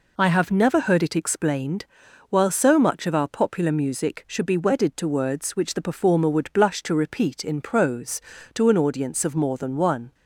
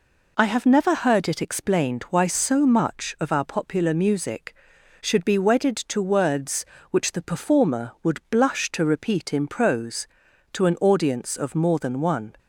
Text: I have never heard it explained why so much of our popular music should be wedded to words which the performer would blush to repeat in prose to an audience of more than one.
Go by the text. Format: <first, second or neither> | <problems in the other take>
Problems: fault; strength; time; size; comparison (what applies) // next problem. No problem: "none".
second | says "while" for "why"; at 2.2 s